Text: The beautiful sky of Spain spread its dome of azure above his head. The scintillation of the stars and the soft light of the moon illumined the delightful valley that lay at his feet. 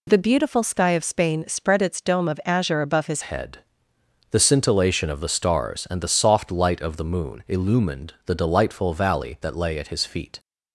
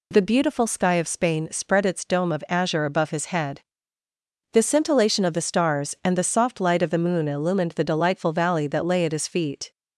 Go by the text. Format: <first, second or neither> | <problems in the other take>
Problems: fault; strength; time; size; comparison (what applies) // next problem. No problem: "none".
second | changes voice at "head"; from 3.2 s on; 7.1 s long